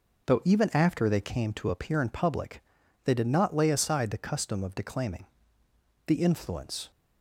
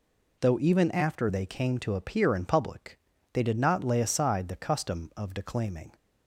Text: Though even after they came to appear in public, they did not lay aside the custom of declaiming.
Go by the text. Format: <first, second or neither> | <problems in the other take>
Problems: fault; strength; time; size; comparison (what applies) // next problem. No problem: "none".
second | goes on to say "The influence"; noticeable; from 6.0 s on; 0.84 s long